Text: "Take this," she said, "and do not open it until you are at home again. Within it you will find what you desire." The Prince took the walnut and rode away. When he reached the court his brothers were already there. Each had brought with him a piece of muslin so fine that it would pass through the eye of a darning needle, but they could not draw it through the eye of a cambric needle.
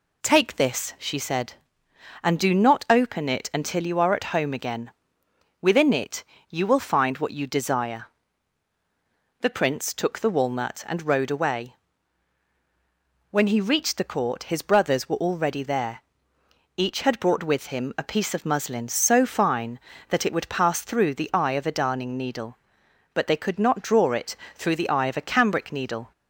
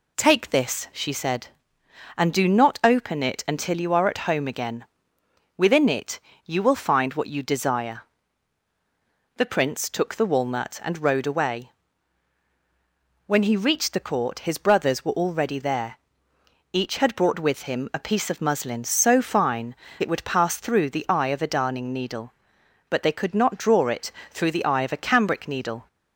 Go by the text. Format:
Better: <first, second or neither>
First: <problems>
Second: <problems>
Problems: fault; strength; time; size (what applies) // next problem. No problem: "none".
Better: first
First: pauses between "it" and "you"; slight; at 6.2 s; 0.26 s long // pauses between "it" and "through"; slight; at 24.3 s; 0.20 s long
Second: pauses between "it" and "you"; slight; at 6.1 s; 0.26 s long // skips "that"; at 19.8 s // pauses between "it" and "through"; slight; at 24.1 s; 0.20 s long